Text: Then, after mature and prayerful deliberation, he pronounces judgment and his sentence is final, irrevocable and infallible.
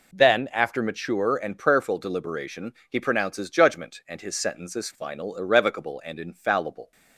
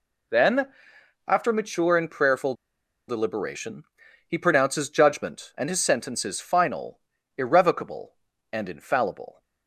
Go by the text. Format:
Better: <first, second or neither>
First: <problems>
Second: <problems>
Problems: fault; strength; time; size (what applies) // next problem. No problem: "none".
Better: first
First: none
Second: pauses between "prayerful" and "deliberation"; noticeable; at 2.5 s; 0.54 s long